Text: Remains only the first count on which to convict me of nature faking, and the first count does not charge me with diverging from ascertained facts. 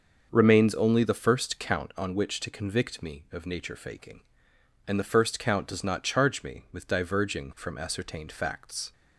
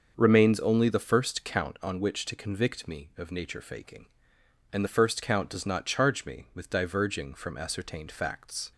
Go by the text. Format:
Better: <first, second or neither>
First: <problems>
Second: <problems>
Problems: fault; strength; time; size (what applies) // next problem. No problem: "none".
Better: neither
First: starts louder than the rest; until 1.3 s; 6.5 dB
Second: starts louder than the rest; until 1.1 s; 6.5 dB